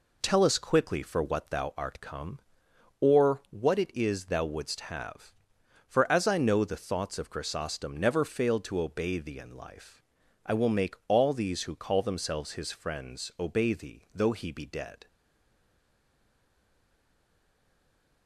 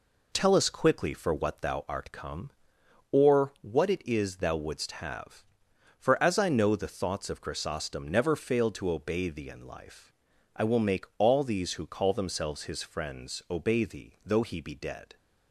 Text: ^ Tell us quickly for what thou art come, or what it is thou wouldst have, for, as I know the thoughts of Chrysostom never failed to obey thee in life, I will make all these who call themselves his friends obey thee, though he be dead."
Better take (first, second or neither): second